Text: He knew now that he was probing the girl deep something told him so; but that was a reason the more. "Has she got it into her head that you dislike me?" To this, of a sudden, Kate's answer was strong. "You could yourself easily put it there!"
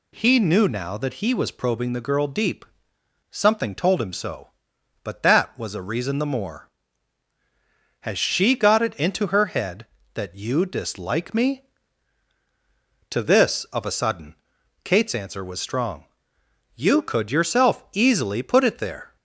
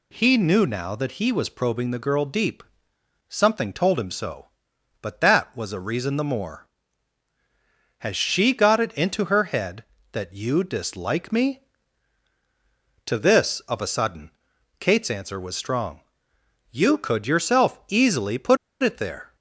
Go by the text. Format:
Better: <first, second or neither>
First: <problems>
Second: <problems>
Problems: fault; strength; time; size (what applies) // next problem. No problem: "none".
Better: first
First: pauses between "deep" and "something"; noticeable; at 2.6 s; 0.68 s long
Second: pauses between "deep" and "something"; noticeable; at 2.6 s; 0.68 s long // pauses between "put" and "it"; slight; at 18.5 s; 0.26 s long